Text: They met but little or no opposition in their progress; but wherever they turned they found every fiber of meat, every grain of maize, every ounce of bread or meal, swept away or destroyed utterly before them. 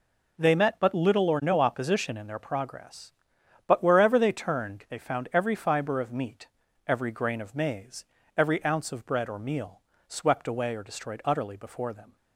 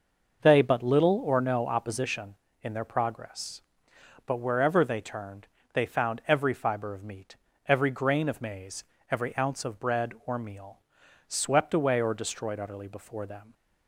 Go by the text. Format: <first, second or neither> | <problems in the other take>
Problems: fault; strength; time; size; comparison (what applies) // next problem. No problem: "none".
first | skips "met"; at 0.6 s // pauses between "turned" and "they"; slight; at 5.4 s; 0.24 s long